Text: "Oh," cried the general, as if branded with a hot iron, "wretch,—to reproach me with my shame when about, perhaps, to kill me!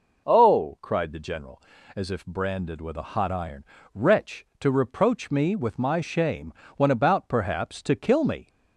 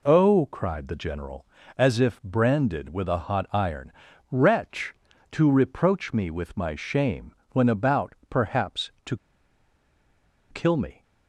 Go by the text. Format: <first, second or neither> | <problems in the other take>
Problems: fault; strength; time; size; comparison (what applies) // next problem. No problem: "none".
first | pauses between "shame" and "when"; slight; at 7.3 s; 0.20 s long; slight in the first // pauses between "to" and "kill"; strong; at 9.1 s; 1.3 s long